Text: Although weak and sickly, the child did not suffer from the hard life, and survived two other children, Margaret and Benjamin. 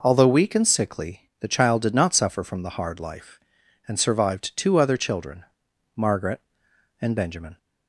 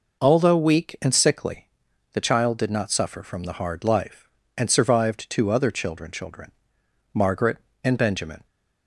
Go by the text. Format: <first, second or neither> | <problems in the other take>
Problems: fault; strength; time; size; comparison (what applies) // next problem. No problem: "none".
first | says "children" twice; at 6.0 s